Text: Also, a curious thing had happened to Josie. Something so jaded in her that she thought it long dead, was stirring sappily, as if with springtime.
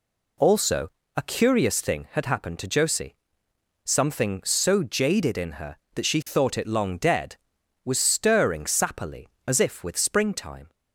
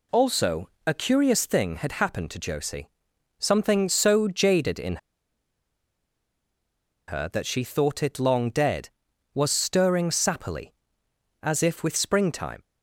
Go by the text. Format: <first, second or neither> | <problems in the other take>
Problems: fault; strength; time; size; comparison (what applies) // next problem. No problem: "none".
first | pauses between "in" and "her"; strong; at 4.9 s; 2.1 s long